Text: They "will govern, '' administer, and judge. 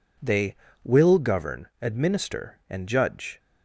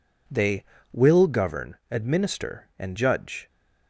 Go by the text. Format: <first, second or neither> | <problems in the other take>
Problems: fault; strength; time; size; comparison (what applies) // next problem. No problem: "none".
neither | none